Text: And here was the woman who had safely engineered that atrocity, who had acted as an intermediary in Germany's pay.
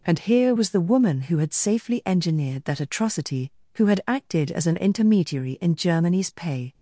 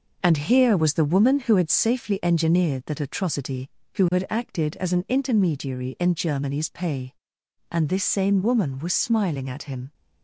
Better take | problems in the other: first | goes on to say "And this same woman was smiling at him"; strong; from 7.6 s on; 2.2 s long

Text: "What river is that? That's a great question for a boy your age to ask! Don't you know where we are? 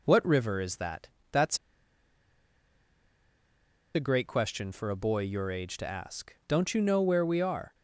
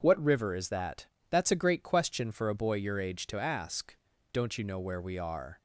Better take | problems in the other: second | pauses between "That's" and "a"; strong; at 1.5 s; 2.3 s long

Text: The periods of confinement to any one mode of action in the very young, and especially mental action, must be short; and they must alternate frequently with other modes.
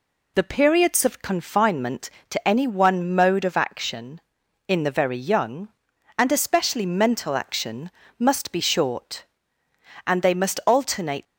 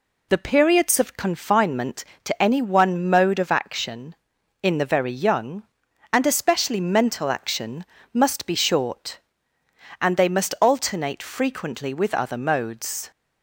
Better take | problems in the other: second | stops before "frequently with other modes"; at 11.2 s

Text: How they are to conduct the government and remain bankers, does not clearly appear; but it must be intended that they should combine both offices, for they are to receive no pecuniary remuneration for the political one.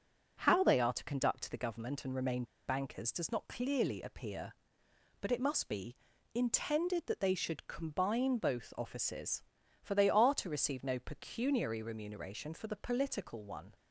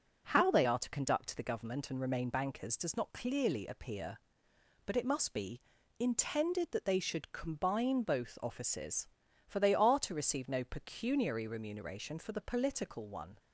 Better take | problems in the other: second | starts louder than the rest; noticeable; until 1.4 s; 6 dB; noticeable in the second // pauses between "remain" and "bankers"; slight; at 2.4 s; 0.23 s long // pauses between "be" and "intended"; at 5.9 s; 0.40 s long; also in the second

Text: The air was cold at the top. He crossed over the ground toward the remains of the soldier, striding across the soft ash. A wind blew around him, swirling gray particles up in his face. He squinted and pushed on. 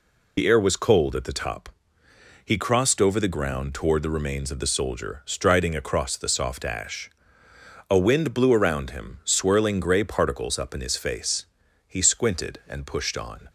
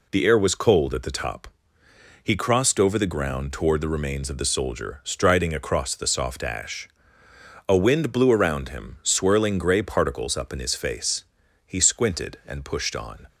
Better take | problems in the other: second | loses the start of "The"; at 0.3 s; 55 ms

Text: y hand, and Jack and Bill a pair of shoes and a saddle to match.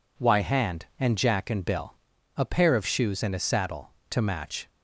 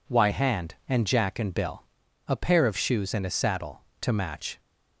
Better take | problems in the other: neither | pauses between "Bill" and "a"; the same in both

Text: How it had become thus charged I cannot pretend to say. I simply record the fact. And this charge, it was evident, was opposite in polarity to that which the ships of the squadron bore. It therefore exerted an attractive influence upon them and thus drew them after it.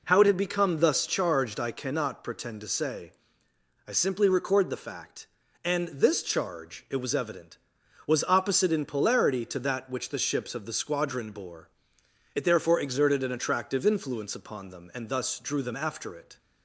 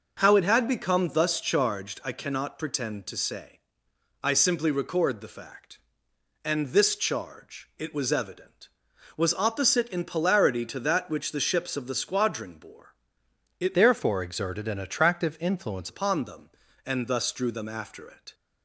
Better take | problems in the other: first | changes voice from "therefore" to "influence"; from 13.7 to 15.9 s; 2.2 s long

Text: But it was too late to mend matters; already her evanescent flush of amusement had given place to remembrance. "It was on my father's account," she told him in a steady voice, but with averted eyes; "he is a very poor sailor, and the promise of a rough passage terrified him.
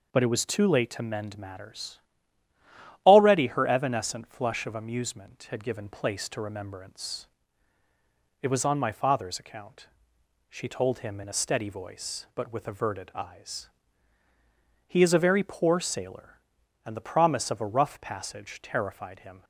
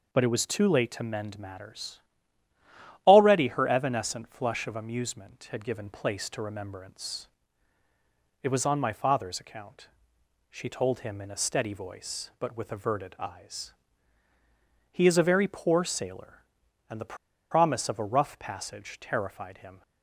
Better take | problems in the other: first | pauses between "the" and "promise"; at 17.1 s; 0.36 s long

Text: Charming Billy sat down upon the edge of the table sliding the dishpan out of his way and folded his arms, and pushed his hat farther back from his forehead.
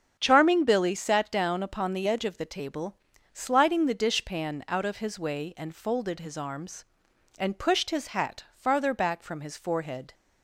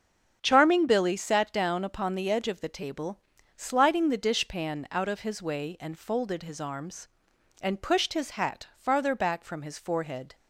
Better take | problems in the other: neither | starts louder than the rest; strong; the same in both // pauses between "table" and "sliding"; the same in both

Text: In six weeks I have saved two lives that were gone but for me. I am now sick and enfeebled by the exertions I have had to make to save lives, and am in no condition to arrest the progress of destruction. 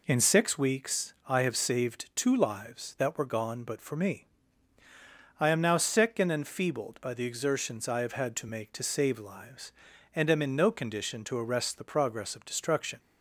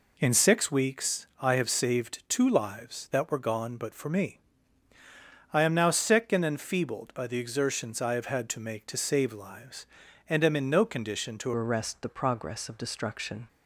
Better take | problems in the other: first | changes voice at "arrest"; from 11.5 s on; 1.9 s long

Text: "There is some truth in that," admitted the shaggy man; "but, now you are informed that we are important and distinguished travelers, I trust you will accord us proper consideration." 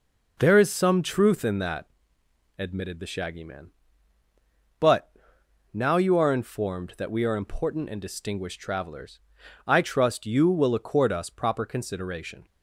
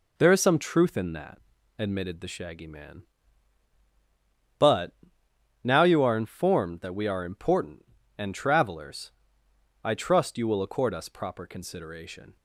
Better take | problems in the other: first | skips "distinguished"; at 8.3 s

